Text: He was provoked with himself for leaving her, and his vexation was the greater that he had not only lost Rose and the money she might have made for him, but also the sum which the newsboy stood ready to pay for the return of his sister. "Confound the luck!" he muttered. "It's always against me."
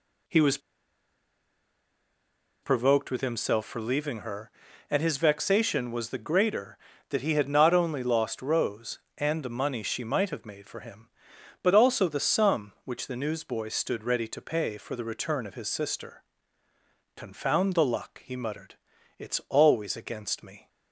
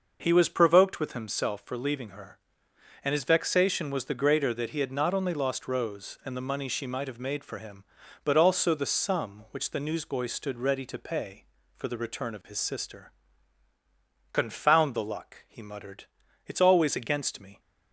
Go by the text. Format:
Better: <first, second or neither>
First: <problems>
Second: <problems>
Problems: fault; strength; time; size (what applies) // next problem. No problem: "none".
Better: second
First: pauses between "was" and "provoked"; strong; at 0.5 s; 2.0 s long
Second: none